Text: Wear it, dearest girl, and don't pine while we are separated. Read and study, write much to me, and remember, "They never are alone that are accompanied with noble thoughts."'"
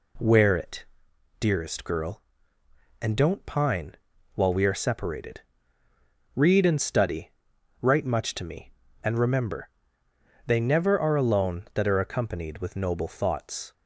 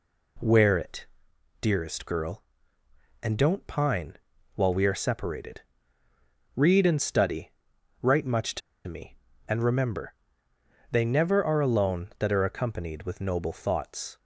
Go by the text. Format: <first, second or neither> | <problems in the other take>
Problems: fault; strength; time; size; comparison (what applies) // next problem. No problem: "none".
first | pauses between "pine" and "while"; at 4.1 s; 0.38 s long; also in the first // pauses between "to" and "me"; slight; at 8.6 s; 0.27 s long